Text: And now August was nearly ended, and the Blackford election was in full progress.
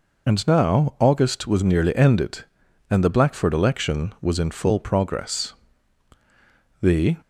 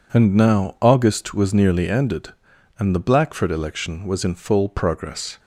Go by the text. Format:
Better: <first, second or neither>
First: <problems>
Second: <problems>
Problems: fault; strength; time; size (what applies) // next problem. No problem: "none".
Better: second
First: goes on to say "The"; slight; from 6.8 s on; 0.38 s long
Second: none